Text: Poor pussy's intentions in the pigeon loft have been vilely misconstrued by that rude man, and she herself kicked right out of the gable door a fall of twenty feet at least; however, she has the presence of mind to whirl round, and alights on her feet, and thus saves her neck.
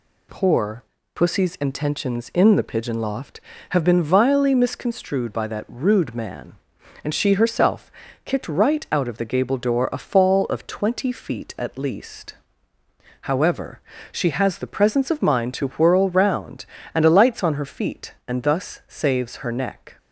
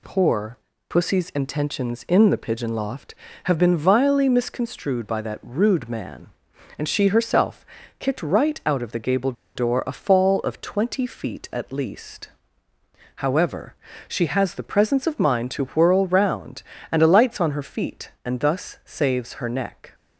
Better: first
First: pauses between "Poor" and "pussy's"; slight; at 0.8 s; 0.32 s long // pauses between "herself" and "kicked"; slight; at 7.9 s; 0.32 s long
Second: pauses between "Poor" and "pussy's"; slight; at 0.5 s; 0.32 s long // pauses between "herself" and "kicked"; slight; at 7.6 s; 0.32 s long // pauses between "gable" and "door"; slight; at 9.3 s; 0.23 s long

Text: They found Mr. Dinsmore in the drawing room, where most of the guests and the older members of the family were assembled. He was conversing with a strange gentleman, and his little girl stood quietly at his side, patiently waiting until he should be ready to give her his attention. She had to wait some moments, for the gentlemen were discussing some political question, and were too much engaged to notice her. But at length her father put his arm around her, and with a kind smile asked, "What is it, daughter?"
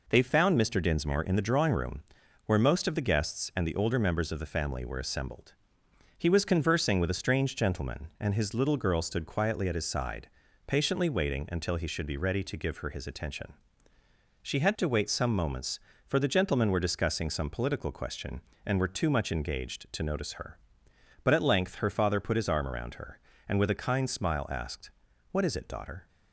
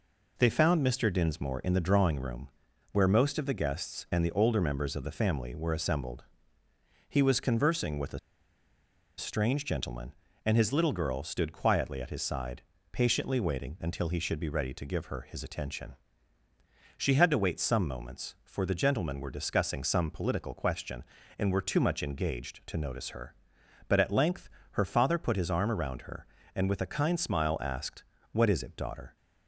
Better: first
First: none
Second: pauses between "a" and "strange"; at 8.1 s; 0.98 s long // pauses between "length" and "her"; slight; at 24.4 s; 0.24 s long

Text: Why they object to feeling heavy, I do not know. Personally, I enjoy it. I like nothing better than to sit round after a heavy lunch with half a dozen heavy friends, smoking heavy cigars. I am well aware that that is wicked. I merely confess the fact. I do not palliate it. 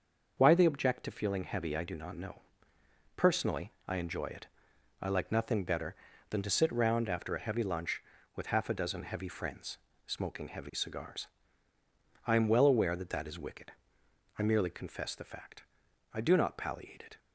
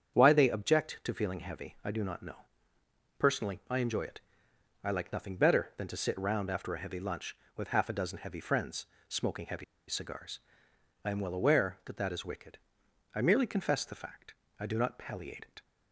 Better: first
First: starts louder than the rest; until 1.3 s; 6.5 dB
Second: starts louder than the rest; strong; until 1.1 s; 7.5 dB // pauses between "heavy" and "cigars"; slight; at 9.6 s; 0.23 s long

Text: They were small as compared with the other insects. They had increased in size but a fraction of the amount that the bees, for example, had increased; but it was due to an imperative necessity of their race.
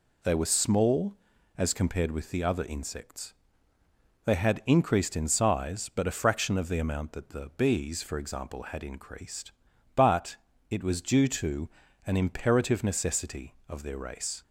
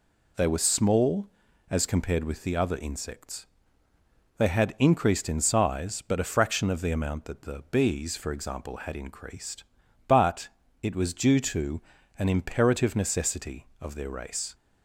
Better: neither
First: pauses between "but" and "it"; slight; at 10.3 s; 0.34 s long // pauses between "to" and "an"; slight; at 11.6 s; 0.36 s long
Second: pauses between "but" and "it"; slight; at 10.4 s; 0.34 s long // pauses between "to" and "an"; slight; at 11.8 s; 0.36 s long

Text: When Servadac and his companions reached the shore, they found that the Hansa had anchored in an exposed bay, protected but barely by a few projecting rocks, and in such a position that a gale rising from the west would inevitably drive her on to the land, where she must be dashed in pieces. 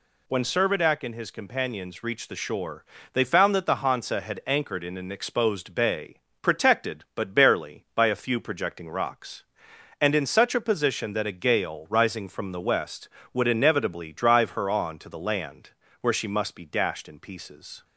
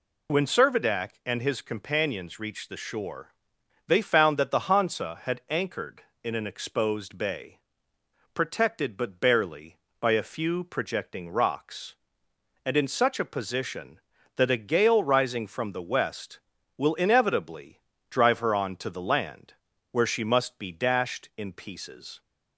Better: first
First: none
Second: says "will" for "would"; at 16.7 s // pauses between "inevitably" and "drive"; slight; at 17.8 s; 0.28 s long

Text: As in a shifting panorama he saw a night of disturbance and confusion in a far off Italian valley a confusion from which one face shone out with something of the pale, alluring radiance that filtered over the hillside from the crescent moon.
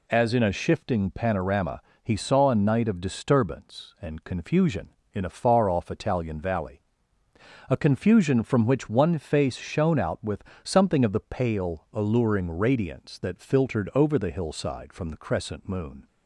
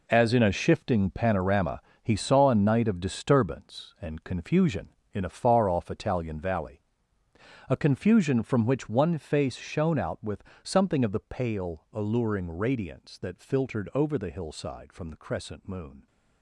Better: first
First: pauses between "panorama" and "he"; slight; at 1.8 s; 0.20 s long // pauses between "valley" and "a"; noticeable; at 6.8 s; 0.88 s long // pauses between "with" and "something"; slight; at 10.4 s; 0.20 s long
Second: gets quieter; strong; throughout; 11.5 dB // pauses between "panorama" and "he"; slight; at 1.8 s; 0.20 s long // pauses between "valley" and "a"; noticeable; at 6.8 s; 0.88 s long // pauses between "with" and "something"; slight; at 10.4 s; 0.20 s long

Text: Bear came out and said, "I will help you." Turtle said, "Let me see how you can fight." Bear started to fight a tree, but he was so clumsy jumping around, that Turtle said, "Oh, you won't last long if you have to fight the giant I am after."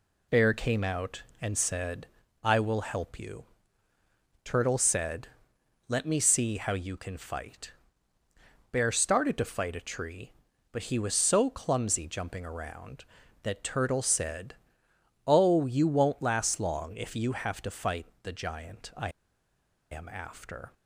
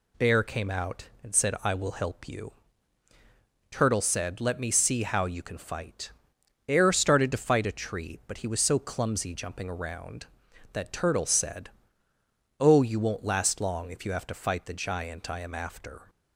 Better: second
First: pauses between "fight" and "the"; slight; at 18.0 s; 0.16 s long // pauses between "I" and "am"; noticeable; at 19.0 s; 0.81 s long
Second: none

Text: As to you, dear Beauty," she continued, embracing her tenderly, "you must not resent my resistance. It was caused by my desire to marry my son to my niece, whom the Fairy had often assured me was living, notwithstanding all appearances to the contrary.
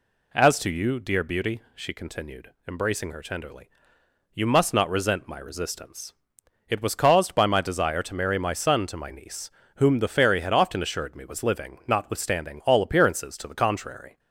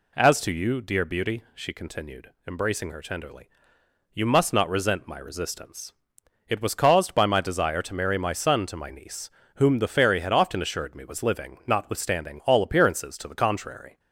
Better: neither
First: none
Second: none

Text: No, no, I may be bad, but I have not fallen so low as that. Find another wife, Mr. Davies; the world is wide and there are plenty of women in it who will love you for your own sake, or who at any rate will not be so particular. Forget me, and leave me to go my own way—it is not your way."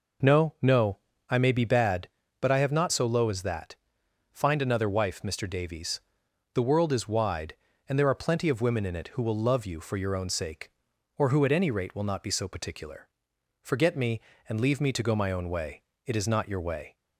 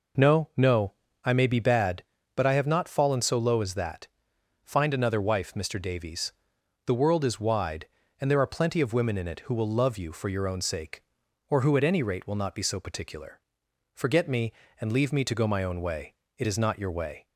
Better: second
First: skips "fallen"; at 2.9 s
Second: none

